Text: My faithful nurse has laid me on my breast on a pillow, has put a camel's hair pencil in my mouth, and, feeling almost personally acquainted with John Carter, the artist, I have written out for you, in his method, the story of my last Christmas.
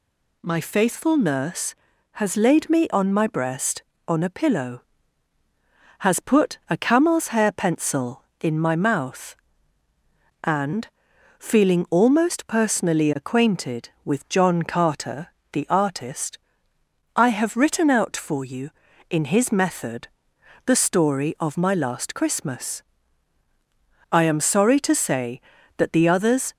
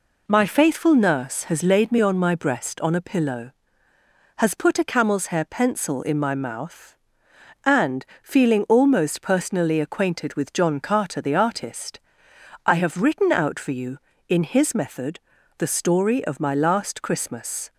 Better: second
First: goes on to say "I am sorry to say that the others"; strong; from 24.1 s on; 2.4 s long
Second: none

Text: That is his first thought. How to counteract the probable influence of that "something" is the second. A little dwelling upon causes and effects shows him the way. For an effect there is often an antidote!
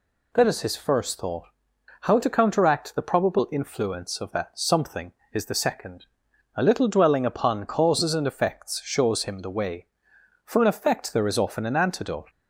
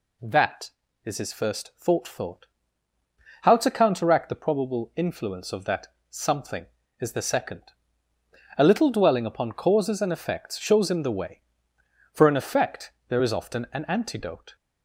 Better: first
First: none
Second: says "thought" twice; at 2.0 s // pauses between "that" and "something"; slight; at 5.8 s; 0.20 s long // pauses between "effect" and "there"; slight; at 12.9 s; 0.16 s long

